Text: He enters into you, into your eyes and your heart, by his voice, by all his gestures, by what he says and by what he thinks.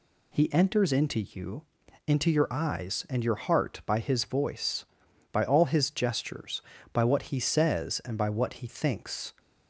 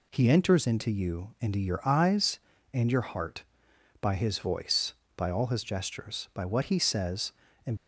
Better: first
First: none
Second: stops before "by what he thinks"; at 7.7 s

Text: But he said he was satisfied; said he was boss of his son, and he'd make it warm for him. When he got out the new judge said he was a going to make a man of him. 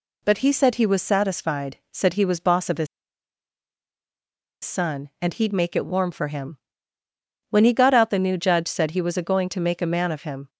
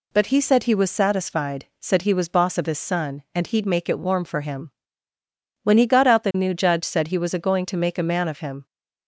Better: second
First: pauses between "his" and "son"; strong; at 2.8 s; 1.7 s long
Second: none

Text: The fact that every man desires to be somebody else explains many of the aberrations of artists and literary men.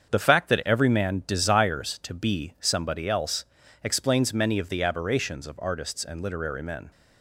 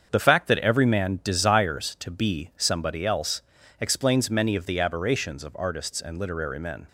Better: neither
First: starts louder than the rest; until 1.1 s; 7 dB // pauses between "else" and "explains"; at 3.4 s; 0.40 s long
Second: starts louder than the rest; until 1.1 s; 7 dB // pauses between "else" and "explains"; at 3.4 s; 0.40 s long

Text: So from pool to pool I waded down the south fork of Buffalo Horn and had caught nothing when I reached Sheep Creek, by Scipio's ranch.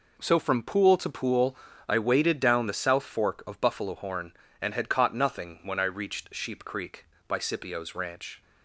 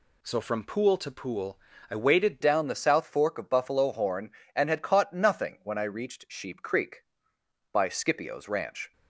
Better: first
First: pauses between "pool" and "I"; slight; at 1.5 s; 0.32 s long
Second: pauses between "pool" and "I"; slight; at 1.5 s; 0.32 s long // changes voice at "down"; from 2.4 s on; 6.5 s long

